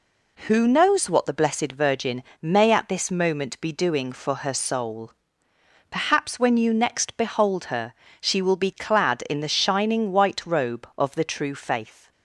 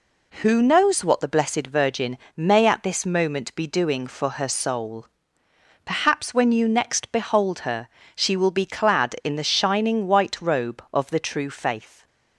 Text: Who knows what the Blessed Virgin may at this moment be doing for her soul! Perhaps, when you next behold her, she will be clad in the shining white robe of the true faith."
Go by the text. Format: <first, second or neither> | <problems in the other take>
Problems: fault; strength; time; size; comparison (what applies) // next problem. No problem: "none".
neither | pauses between "Virgin" and "may"; slight; the same in both